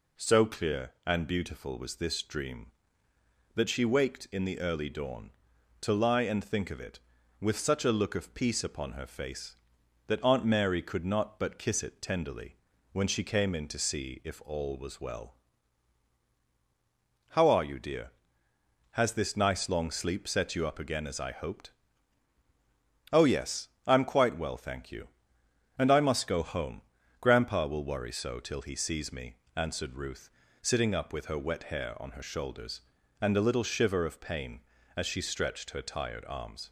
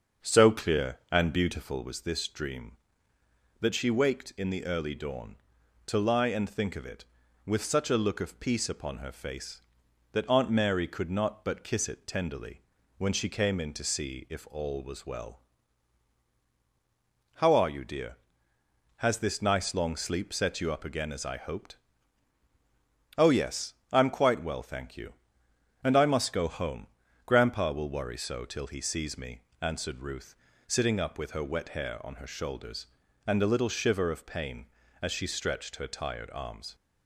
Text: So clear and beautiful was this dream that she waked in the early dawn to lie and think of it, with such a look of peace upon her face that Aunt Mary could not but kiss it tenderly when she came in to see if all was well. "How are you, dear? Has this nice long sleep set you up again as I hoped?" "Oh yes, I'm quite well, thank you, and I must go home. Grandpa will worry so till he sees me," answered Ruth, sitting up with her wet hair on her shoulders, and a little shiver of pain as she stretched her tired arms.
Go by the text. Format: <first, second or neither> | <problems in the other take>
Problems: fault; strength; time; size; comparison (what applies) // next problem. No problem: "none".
first | starts louder than the rest; until 1.9 s; 6.5 dB // pauses between "tenderly" and "when"; at 12.6 s; 0.38 s long; also in the first